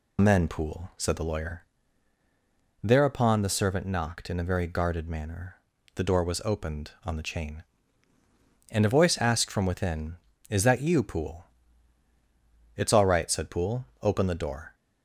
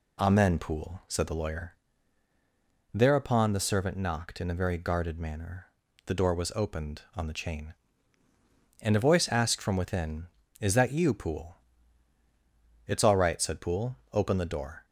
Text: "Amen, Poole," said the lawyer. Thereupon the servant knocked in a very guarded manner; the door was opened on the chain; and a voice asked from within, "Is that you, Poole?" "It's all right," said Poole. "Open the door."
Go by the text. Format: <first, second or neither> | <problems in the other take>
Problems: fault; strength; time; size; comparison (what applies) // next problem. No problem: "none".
second | loses the start of "Amen"; at 0.1 s; 115 ms